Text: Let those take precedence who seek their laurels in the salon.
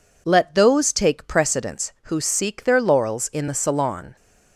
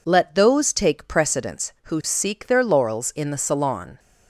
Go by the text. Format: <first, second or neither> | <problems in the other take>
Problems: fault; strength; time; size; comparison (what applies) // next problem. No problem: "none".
neither | none